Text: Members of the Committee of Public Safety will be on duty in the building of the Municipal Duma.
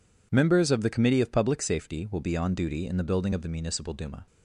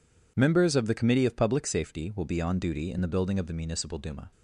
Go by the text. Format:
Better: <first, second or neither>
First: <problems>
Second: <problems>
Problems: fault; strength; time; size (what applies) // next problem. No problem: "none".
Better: neither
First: none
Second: none